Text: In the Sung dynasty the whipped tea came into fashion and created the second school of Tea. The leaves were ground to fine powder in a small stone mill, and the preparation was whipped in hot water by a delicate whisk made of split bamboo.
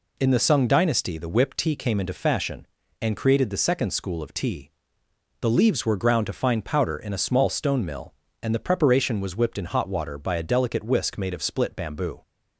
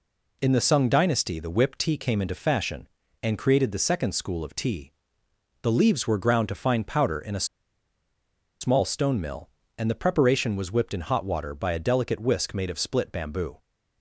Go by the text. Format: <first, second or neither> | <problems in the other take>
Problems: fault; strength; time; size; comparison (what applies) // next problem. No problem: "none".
first | pauses between "a" and "small"; at 7.4 s; 1.1 s long